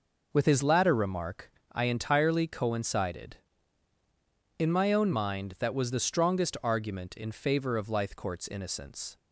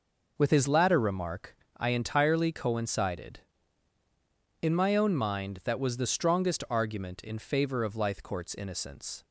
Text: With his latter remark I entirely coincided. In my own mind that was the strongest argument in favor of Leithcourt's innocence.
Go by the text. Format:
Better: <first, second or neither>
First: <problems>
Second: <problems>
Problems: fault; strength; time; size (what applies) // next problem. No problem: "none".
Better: neither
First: pauses between "remark" and "I"; slight; at 1.5 s; 0.22 s long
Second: pauses between "remark" and "I"; slight; at 1.5 s; 0.22 s long